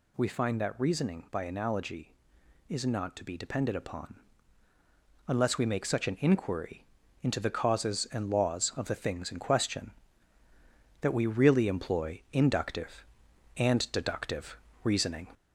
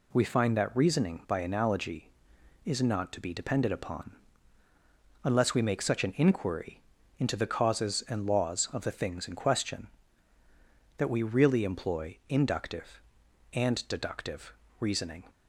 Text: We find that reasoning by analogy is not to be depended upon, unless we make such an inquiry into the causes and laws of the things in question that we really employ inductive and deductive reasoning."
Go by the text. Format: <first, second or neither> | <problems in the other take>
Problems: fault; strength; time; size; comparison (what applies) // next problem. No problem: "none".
second | gets louder; slight; throughout; 3 dB // pauses between "inquiry" and "into"; at 6.8 s; 0.38 s long; also in the second // pauses between "deductive" and "reasoning"; slight; at 14.5 s; 0.28 s long; slight in the second